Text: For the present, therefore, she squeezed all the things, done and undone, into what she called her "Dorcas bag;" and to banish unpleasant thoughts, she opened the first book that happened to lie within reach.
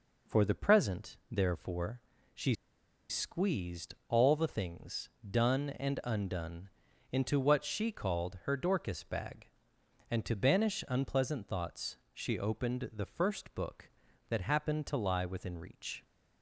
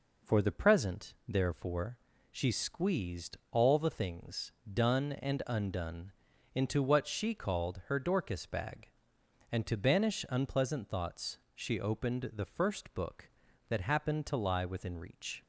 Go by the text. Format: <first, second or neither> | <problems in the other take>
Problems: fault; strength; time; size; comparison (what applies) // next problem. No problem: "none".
second | pauses between "she" and "squeezed"; noticeable; at 2.5 s; 0.56 s long // pauses between "squeezed" and "all"; slight; at 3.9 s; 0.16 s long; slight in the second